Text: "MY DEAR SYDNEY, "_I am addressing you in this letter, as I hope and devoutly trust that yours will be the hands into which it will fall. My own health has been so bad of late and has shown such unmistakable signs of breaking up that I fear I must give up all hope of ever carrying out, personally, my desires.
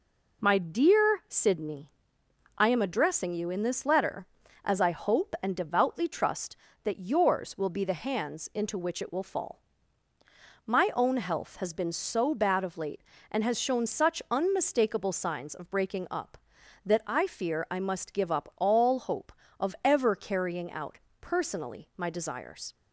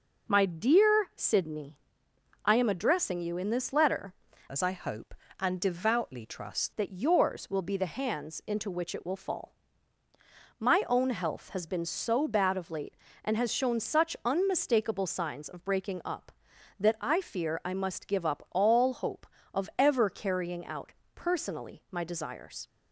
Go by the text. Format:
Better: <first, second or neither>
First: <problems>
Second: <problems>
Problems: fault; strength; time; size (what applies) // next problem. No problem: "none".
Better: first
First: none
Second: changes voice from "as" to "trust"; from 4.4 to 6.7 s; 2.3 s long